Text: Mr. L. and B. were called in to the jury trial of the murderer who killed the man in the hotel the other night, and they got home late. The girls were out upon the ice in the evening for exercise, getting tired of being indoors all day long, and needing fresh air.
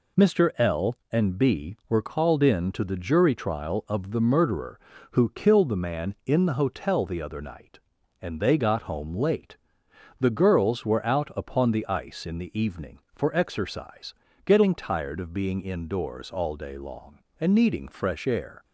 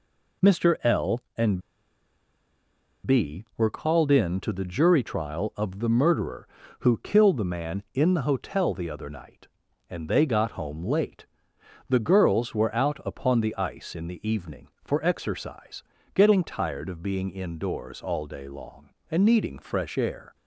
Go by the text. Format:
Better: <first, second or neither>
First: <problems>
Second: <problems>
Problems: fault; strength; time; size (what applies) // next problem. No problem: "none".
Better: first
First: none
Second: pauses between "and" and "B"; strong; at 1.6 s; 1.4 s long